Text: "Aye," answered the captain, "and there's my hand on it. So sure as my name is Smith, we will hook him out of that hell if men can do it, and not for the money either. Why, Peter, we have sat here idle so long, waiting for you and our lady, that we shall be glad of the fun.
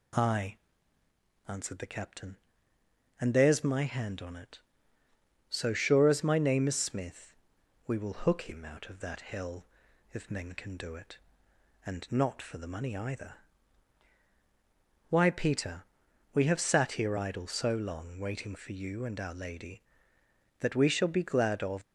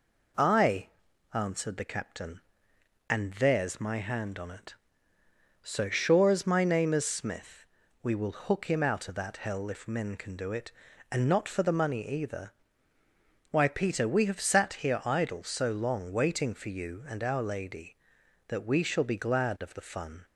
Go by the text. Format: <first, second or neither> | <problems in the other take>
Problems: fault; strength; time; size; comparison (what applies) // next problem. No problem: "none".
second | pauses between "hell" and "if"; noticeable; at 9.6 s; 0.48 s long // stops before "the fun"; at 21.8 s